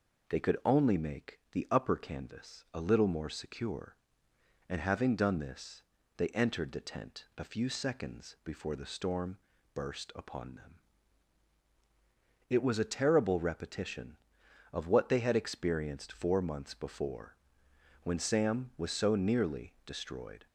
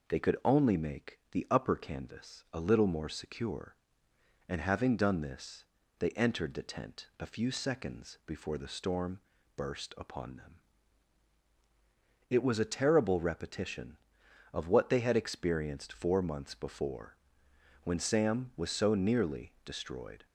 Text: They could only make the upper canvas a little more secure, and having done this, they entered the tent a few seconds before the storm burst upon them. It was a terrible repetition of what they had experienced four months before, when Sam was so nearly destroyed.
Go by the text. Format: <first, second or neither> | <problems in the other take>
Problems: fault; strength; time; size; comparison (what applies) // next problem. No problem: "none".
neither | pauses between "storm" and "burst"; slight; the same in both